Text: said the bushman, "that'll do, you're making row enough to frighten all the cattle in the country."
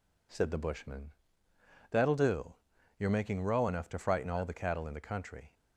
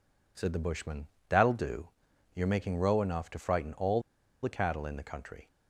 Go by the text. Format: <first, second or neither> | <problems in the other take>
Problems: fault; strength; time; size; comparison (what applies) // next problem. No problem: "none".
first | pauses between "all" and "the"; at 4.0 s; 0.41 s long